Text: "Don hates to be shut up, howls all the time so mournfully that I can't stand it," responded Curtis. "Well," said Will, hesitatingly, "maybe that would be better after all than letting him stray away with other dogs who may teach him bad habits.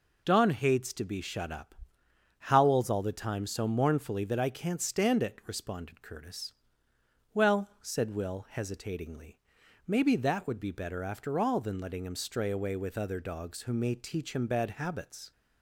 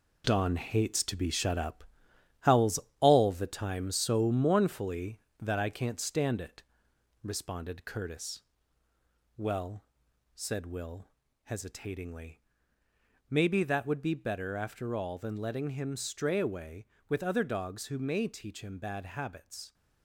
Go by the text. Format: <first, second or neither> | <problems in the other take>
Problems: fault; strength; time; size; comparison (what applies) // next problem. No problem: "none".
first | gets quieter; strong; throughout; 7.5 dB // pauses between "howls" and "all"; slight; at 2.7 s; 0.20 s long